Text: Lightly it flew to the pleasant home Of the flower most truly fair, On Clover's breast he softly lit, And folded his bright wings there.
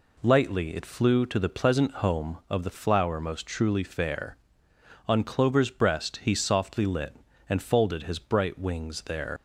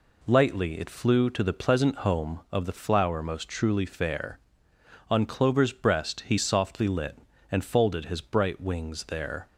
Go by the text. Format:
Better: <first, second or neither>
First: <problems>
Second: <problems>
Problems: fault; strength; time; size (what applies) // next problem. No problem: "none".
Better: second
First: leaves "there" unfinished; at 9.3 s; 85 ms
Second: none